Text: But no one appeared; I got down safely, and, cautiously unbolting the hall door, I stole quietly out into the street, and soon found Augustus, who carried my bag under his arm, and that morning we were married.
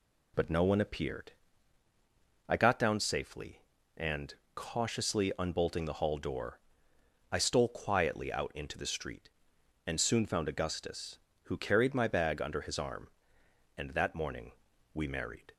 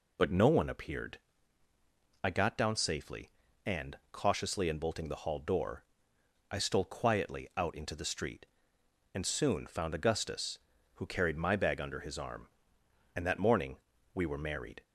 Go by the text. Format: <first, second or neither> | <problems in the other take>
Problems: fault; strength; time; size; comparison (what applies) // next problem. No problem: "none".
second | pauses between "morning" and "we"; at 14.5 s; 0.42 s long; slight in the second // skips "were"; at 15.0 s